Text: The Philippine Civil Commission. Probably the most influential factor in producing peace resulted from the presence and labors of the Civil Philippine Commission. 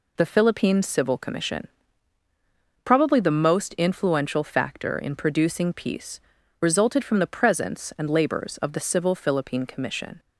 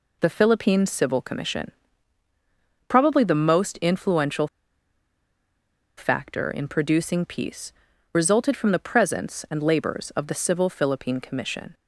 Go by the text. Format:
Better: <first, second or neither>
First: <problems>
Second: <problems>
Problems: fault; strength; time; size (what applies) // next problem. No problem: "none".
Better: first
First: pauses between "peace" and "resulted"; at 6.1 s; 0.40 s long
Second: pauses between "influential" and "factor"; strong; at 4.4 s; 1.5 s long // pauses between "peace" and "resulted"; at 7.7 s; 0.40 s long